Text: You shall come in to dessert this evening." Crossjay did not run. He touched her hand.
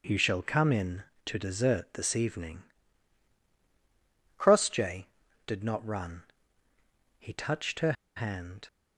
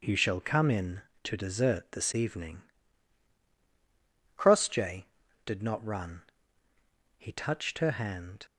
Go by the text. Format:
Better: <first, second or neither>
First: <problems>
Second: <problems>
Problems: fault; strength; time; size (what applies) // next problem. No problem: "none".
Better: second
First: pauses between "her" and "hand"; slight; at 7.9 s; 0.23 s long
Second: none